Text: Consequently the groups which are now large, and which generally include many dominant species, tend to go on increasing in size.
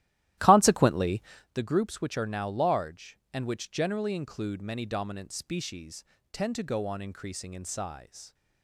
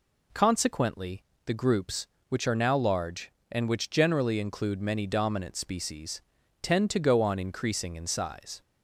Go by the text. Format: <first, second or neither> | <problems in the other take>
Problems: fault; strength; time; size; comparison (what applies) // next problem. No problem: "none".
second | starts louder than the rest; strong; until 1.6 s; 14.5 dB // pauses between "Consequently" and "the"; slight; at 1.2 s; 0.32 s long; slight in the second